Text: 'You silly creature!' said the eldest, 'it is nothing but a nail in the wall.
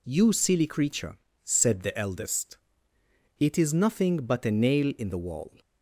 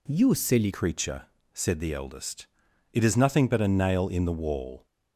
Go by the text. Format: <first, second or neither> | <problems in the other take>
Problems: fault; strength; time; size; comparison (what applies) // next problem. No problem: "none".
first | changes voice at "creature"; from 0.7 s on; 4.1 s long